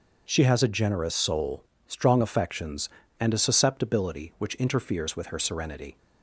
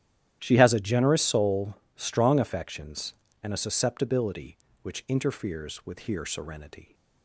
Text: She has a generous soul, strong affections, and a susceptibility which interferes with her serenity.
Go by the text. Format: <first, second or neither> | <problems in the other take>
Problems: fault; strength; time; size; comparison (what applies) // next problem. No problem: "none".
first | starts louder than the rest; strong; until 1.4 s; 12 dB // says "here" for "her"; at 5.9 s